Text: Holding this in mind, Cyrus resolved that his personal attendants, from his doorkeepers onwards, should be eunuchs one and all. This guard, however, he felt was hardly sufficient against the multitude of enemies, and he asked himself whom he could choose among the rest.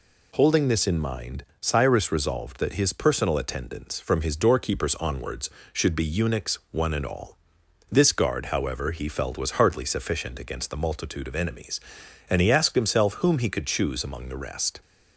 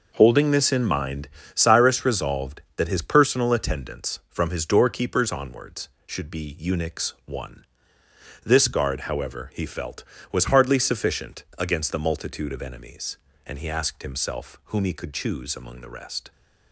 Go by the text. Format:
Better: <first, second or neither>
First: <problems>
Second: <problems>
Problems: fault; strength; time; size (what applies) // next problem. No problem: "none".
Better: first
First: none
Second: skips "and all"; at 8.0 s